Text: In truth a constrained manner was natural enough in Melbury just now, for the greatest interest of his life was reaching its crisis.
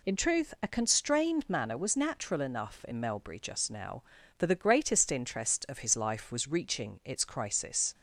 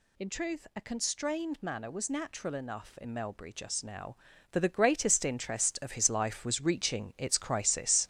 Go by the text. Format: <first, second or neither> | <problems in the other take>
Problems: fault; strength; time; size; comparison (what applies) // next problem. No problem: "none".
first | gets louder; strong; throughout; 7.5 dB